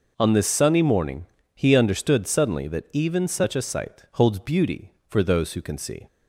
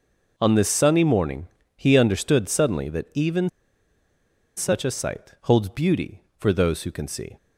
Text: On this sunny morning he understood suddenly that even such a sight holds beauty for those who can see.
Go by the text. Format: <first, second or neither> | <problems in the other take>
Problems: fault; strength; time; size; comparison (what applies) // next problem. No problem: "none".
first | pauses between "morning" and "he"; slight; at 1.4 s; 0.32 s long; slight in the first // pauses between "even" and "such"; at 3.4 s; 1.0 s long